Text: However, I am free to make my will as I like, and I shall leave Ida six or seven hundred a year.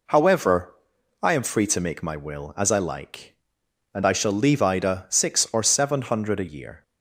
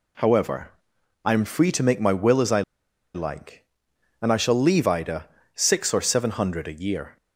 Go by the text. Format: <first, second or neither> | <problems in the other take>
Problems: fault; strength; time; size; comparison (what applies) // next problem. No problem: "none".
first | pauses between "I" and "like"; noticeable; at 2.6 s; 0.52 s long // pauses between "Ida" and "six"; slight; at 5.2 s; 0.28 s long